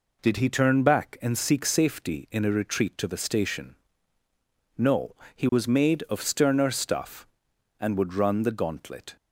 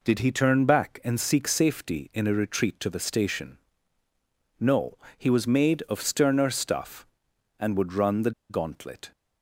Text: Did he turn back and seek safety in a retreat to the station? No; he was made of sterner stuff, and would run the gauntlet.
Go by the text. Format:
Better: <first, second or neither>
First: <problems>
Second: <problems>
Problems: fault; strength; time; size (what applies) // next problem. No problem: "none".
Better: first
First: none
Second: pauses between "the" and "gauntlet"; slight; at 8.3 s; 0.18 s long